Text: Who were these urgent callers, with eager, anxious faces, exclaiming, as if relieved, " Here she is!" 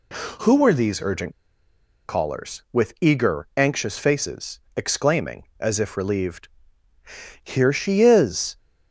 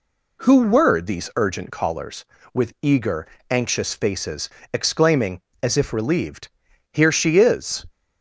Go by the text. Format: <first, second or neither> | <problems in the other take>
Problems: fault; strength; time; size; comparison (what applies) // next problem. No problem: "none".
second | pauses between "urgent" and "callers"; noticeable; at 1.3 s; 0.74 s long